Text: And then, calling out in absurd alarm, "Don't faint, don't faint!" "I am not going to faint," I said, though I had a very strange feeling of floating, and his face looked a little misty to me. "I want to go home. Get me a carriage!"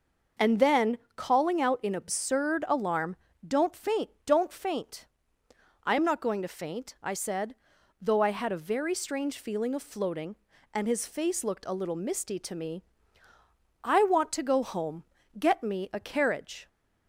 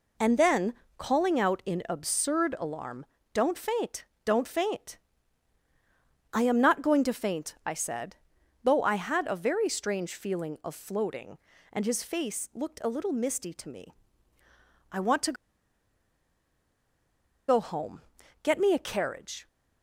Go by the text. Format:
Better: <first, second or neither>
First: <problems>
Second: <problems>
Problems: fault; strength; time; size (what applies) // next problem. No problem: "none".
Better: first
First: none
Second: pauses between "to" and "go"; strong; at 15.3 s; 2.1 s long